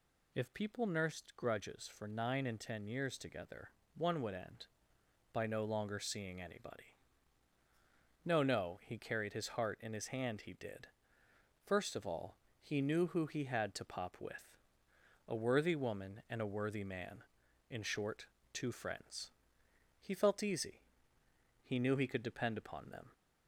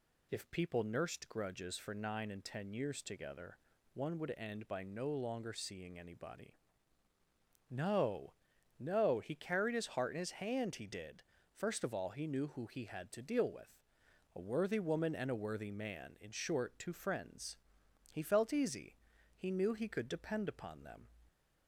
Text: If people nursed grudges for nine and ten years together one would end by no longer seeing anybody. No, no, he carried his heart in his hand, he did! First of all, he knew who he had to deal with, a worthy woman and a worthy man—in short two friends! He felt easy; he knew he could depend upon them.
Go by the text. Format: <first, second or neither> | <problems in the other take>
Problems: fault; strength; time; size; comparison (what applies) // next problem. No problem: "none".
second | pauses between "together" and "one"; slight; at 3.7 s; 0.26 s long; slight in the second // says "pop" for "deal"; at 13.8 s // pauses between "short" and "two"; slight; at 18.2 s; 0.26 s long